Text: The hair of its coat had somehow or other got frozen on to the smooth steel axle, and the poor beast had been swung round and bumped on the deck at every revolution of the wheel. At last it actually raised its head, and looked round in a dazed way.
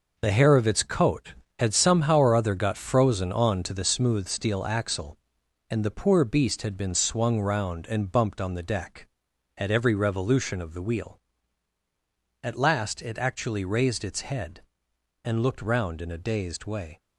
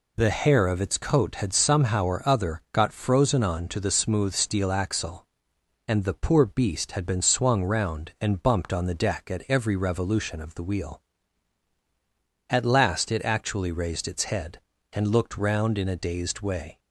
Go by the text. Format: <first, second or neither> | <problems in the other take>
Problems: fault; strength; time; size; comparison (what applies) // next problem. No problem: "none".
second | gets quieter; strong; throughout; 8.5 dB